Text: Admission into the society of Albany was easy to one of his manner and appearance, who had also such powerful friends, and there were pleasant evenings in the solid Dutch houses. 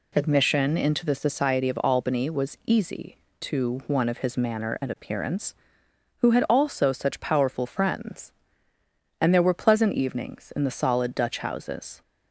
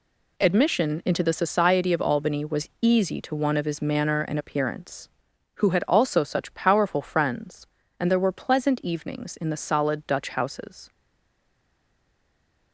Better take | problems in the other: first | stays silent after the last word; noticeable; from 10.8 s on; 1.9 s long

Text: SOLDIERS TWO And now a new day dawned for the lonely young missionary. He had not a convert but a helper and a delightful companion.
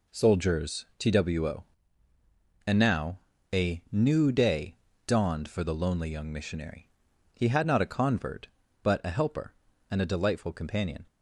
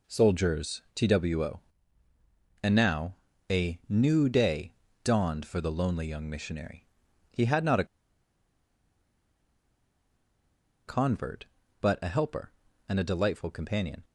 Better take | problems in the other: first | pauses between "now" and "a"; slight; at 3.1 s; 0.34 s long; slight in the first // pauses between "day" and "dawned"; slight; at 4.7 s; 0.28 s long; slight in the first // pauses between "a" and "convert"; strong; at 7.8 s; 3.0 s long

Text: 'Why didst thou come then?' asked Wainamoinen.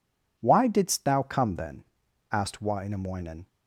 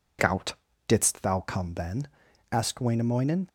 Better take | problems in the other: first | says "Gout" for "Why"; at 0.1 s

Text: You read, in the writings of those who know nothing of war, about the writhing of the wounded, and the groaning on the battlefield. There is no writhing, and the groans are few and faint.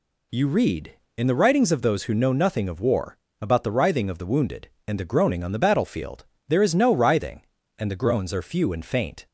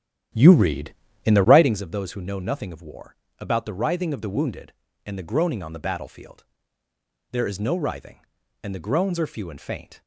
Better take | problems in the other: first | starts louder than the rest; strong; until 1.8 s; 11 dB

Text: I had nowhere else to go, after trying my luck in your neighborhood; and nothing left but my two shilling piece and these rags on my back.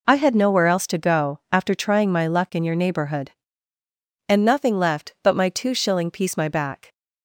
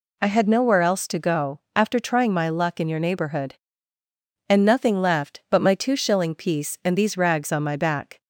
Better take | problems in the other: second | skips "and these rags on"; at 6.3 s

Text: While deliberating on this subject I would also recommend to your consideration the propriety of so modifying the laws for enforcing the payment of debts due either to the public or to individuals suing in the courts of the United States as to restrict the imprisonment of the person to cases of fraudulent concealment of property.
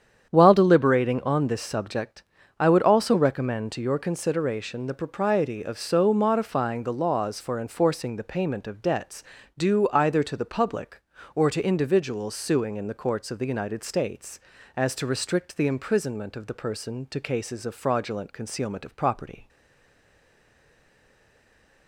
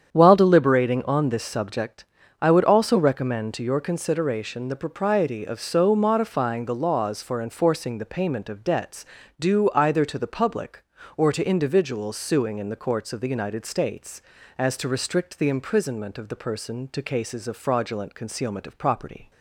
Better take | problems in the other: second | starts louder than the rest; strong; until 1.3 s; 8.5 dB; strong in the second // pauses between "subject" and "I"; slight; at 2.2 s; 0.34 s long; slight in the second // pauses between "debts" and "due"; slight; at 9.2 s; 0.34 s long; slight in the second // stays silent after the last word; from 19.4 s on; 2.4 s long

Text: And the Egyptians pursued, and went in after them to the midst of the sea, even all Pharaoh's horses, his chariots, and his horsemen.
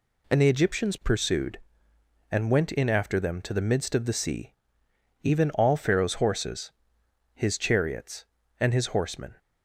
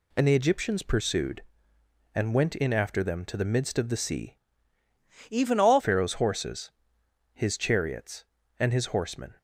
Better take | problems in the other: first | changes voice from "even" to "all"; from 5.3 to 5.8 s; 0.5 s long

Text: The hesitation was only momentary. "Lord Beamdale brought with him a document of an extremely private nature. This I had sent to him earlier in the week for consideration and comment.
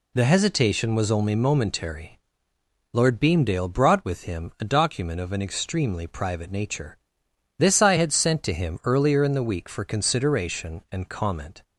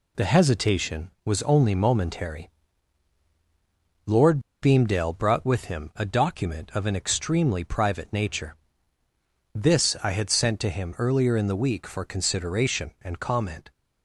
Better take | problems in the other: first | pauses between "Lord" and "Beamdale"; slight; at 4.3 s; 0.22 s long

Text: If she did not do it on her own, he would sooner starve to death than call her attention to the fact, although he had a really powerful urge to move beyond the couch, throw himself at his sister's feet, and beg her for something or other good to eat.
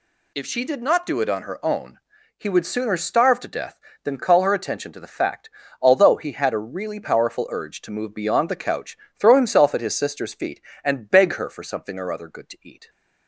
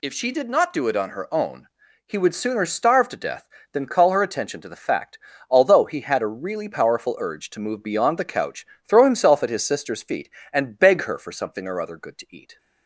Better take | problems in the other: neither | none

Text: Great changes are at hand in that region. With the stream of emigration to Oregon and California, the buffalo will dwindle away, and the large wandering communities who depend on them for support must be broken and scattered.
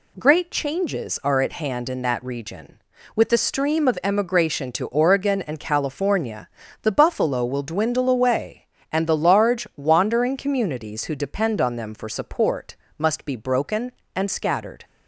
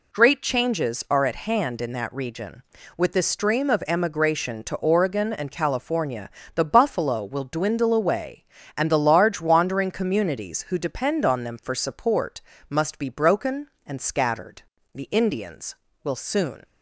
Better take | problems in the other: first | pauses between "support" and "must"; slight; at 12.4 s; 0.28 s long; slight in the first // goes on to say "The Indians will soon"; strong; from 14.9 s on; 1.7 s long

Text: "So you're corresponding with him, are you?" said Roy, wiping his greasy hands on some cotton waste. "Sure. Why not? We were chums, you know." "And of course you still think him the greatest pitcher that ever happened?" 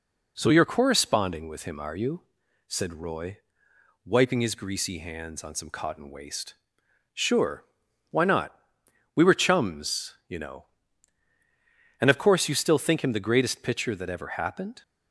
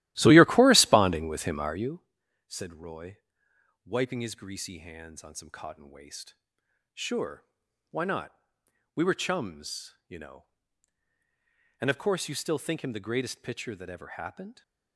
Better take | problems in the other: first | starts louder than the rest; strong; until 2.0 s; 15.5 dB

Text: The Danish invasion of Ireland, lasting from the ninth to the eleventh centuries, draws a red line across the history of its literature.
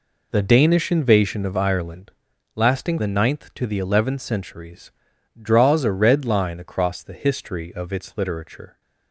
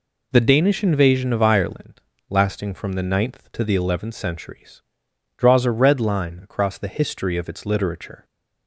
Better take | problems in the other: second | skips "from"; at 2.9 s

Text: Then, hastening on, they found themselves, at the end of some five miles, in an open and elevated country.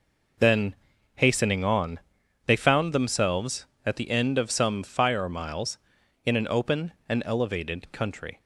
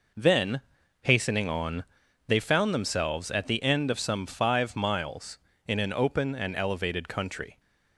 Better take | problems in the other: second | says "fire" for "five"; at 4.8 s

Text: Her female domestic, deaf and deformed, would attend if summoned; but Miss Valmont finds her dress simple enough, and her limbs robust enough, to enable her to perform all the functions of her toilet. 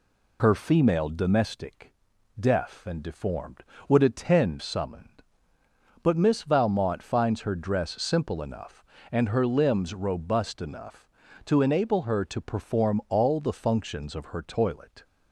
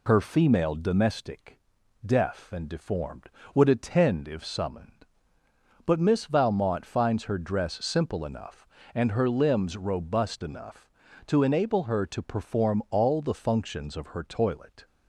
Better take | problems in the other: second | skips "if"; at 4.6 s

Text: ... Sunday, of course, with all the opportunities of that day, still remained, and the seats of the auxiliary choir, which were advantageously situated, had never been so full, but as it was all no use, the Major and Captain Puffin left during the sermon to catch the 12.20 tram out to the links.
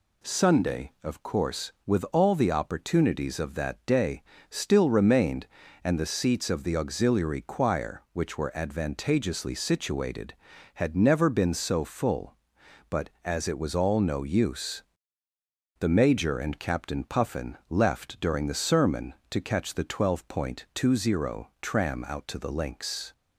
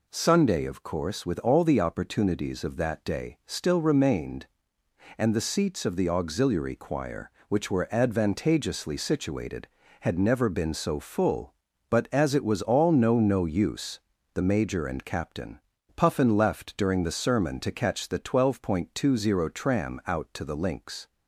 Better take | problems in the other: first | says "no" twice; at 13.1 s // pauses between "Captain" and "Puffin"; slight; at 15.5 s; 0.36 s long

